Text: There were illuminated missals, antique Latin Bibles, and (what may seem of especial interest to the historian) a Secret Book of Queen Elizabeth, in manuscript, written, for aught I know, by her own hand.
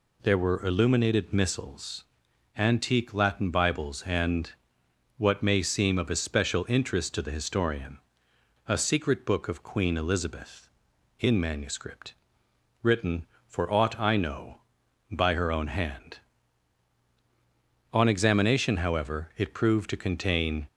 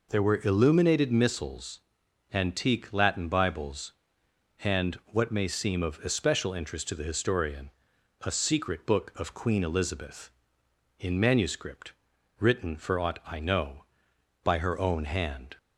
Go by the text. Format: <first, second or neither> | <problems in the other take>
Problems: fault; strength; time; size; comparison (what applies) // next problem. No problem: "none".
second | goes on to say "On examination however it proved to contain"; strong; from 17.9 s on; 2.7 s long